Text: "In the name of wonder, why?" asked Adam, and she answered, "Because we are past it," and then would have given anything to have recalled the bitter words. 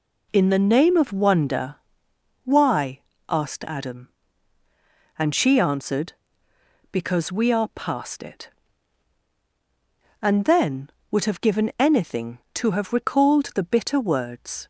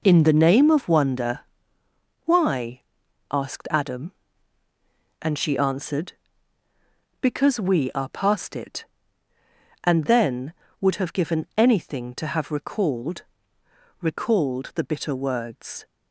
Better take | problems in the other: first | says "recalled" twice; at 13.9 s

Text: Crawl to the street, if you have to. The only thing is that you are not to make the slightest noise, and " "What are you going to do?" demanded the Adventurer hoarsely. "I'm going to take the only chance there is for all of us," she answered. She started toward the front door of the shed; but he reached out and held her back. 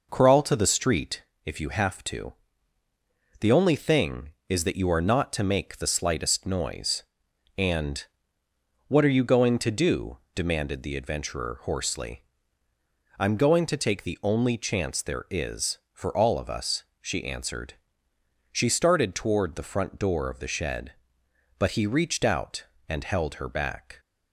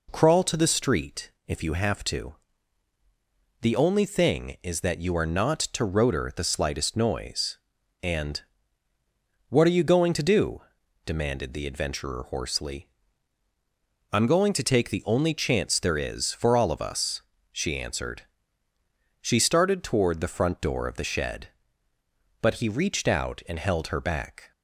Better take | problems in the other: first | says "rotor" for "make"; at 5.8 s

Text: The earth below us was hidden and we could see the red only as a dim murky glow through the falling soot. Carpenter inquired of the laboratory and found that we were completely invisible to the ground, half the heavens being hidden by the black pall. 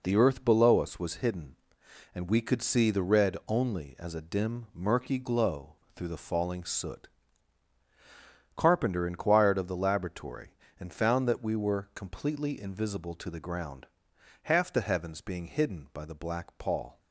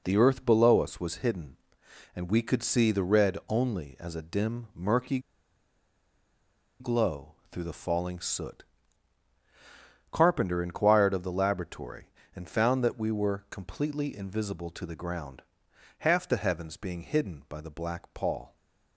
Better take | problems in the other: first | pauses between "murky" and "glow"; strong; at 5.1 s; 1.6 s long // pauses between "glow" and "through"; slight; at 7.3 s; 0.16 s long; slight in the first

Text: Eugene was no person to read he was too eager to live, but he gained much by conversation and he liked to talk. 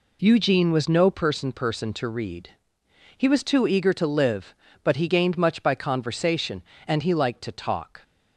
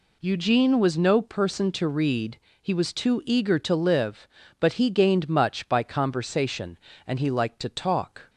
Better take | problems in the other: second | says "person" twice; at 1.5 s // pauses between "read" and "he"; noticeable; at 2.5 s; 0.66 s long; slight in the second

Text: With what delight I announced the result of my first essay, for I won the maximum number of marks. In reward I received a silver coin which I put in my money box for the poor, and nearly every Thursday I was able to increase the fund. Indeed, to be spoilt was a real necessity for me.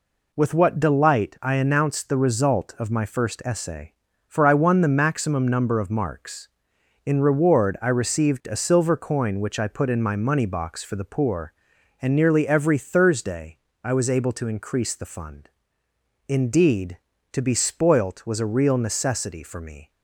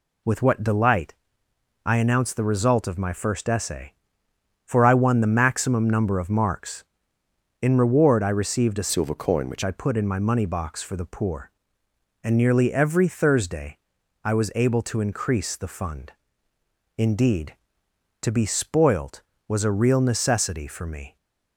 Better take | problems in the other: first | pauses between "delight" and "I"; noticeable; at 1.1 s; 0.72 s long // changes voice from "silver" to "which"; from 8.9 to 9.6 s; 0.7 s long // pauses between "Thursday" and "I"; at 13.7 s; 0.44 s long; slight in the first

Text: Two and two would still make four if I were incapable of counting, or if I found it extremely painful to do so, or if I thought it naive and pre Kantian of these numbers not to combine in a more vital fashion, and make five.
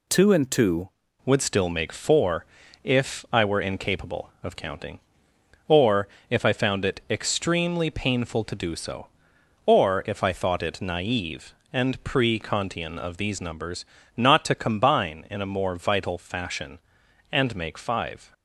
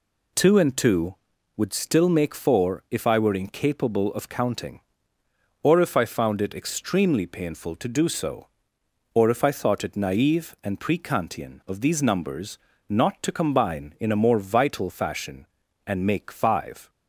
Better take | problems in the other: second | changes voice at "would"; from 1.2 s on; 17.1 s long // pauses between "four" and "if"; at 2.4 s; 0.38 s long // pauses between "or" and "if"; slight; at 6.0 s; 0.24 s long // pauses between "numbers" and "not"; slight; at 13.8 s; 0.32 s long; slight in the second

